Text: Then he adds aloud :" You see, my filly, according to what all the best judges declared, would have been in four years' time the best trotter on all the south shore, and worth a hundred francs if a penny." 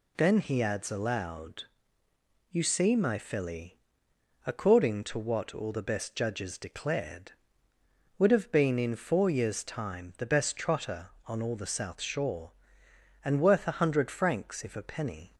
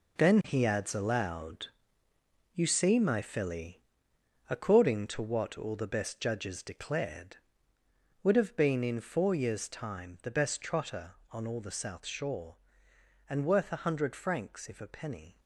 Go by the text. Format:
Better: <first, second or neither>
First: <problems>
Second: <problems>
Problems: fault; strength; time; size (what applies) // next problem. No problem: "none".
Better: first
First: none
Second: gets quieter; throughout; 3.5 dB